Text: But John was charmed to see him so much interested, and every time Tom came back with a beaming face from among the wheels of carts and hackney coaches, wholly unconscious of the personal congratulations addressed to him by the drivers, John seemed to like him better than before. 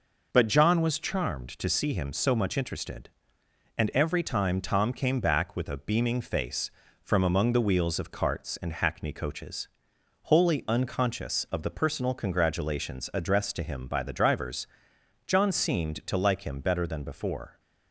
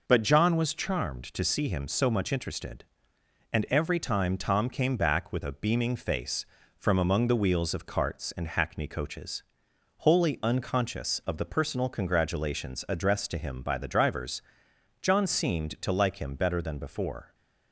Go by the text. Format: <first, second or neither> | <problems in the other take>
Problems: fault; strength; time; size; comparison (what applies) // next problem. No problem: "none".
neither | none